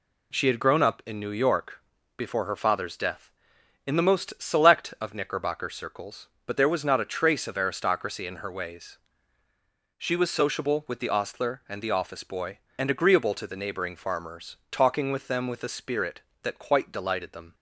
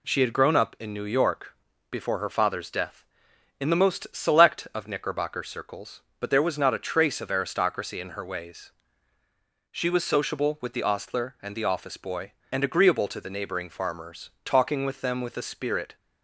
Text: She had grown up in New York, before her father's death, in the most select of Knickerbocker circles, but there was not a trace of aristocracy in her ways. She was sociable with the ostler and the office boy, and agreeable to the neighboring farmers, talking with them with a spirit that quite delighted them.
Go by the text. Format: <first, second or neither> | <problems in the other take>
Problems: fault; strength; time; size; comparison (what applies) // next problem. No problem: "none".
first | stops before "that quite delighted them"; at 15.9 s